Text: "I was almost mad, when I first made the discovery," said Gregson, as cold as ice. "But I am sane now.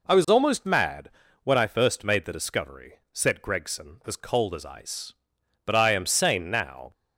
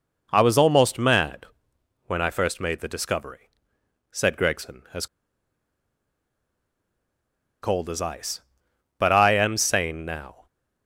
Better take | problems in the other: first | pauses between "as" and "cold"; strong; at 5.0 s; 2.5 s long

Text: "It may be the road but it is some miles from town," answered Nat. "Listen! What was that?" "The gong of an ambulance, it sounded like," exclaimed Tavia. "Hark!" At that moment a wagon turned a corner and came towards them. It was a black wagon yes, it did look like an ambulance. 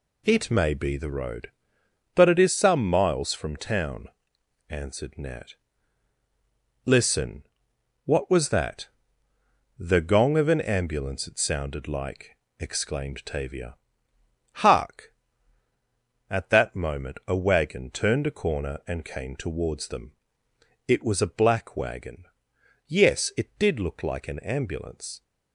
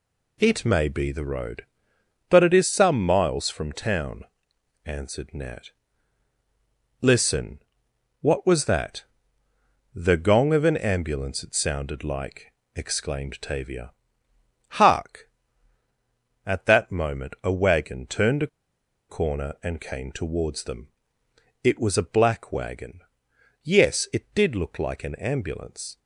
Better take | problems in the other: first | pauses between "a" and "corner"; noticeable; at 18.4 s; 0.61 s long // pauses between "wagon" and "yes"; noticeable; at 23.0 s; 0.60 s long; noticeable in the first

